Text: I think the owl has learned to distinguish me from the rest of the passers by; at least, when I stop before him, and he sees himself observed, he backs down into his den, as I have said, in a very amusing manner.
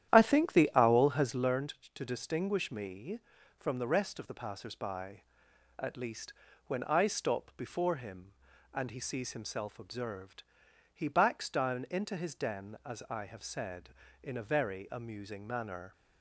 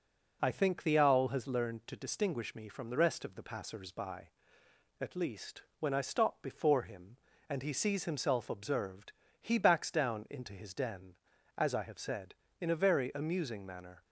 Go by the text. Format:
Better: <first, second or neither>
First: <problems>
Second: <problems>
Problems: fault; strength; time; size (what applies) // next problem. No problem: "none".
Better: second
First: starts louder than the rest; strong; until 1.6 s; 11 dB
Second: none